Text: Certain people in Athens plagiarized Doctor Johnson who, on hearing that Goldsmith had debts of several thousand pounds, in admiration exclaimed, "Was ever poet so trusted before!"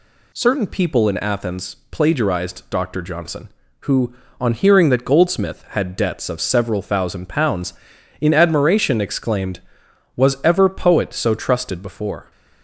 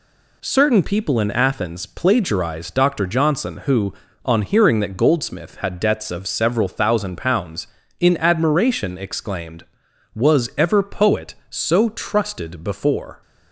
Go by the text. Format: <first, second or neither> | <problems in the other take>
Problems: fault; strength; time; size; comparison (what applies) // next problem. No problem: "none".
neither | none